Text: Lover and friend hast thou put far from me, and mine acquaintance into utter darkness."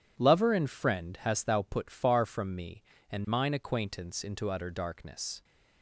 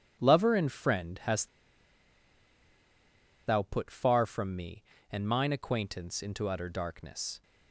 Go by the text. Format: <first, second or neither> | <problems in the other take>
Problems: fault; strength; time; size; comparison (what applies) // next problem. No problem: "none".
first | pauses between "hast" and "thou"; strong; at 1.4 s; 1.9 s long